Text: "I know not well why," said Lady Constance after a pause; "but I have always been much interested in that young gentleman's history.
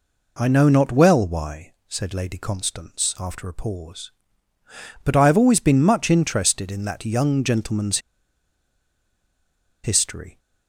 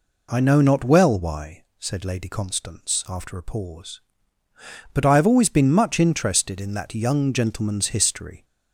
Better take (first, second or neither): second